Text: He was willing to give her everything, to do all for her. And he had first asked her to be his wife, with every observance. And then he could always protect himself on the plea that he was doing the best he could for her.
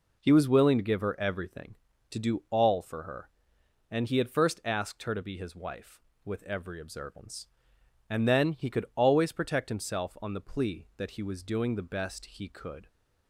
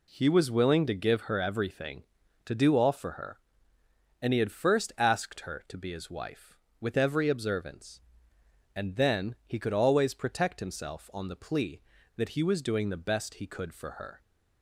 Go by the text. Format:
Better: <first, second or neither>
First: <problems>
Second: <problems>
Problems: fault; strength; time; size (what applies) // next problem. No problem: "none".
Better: second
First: stops before "for her"; at 12.8 s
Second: none